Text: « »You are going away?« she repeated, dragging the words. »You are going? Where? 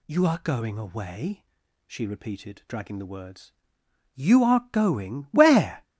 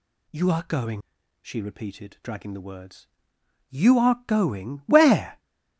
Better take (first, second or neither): first